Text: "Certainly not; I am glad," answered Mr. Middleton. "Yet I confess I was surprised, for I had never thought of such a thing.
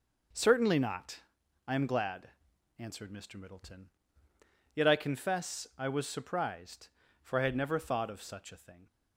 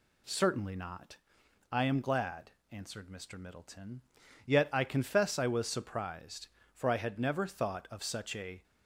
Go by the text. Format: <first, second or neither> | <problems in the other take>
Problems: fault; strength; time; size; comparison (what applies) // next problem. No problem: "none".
first | stops before "thing"; at 8.6 s